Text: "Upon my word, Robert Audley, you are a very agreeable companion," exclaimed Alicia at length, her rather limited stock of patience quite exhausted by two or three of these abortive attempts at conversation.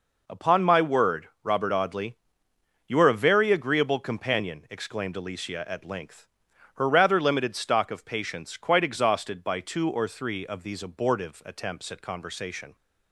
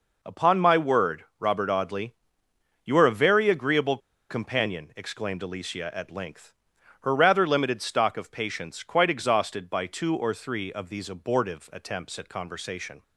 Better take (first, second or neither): first